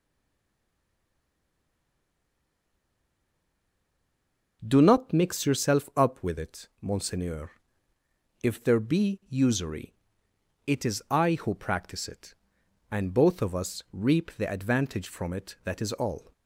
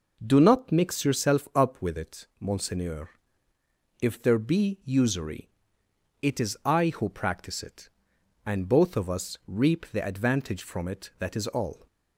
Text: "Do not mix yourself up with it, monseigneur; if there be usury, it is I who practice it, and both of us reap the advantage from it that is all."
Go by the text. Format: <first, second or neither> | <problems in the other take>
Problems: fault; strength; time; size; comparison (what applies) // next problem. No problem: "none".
second | stays silent before the first word; strong; until 4.6 s; 4.6 s long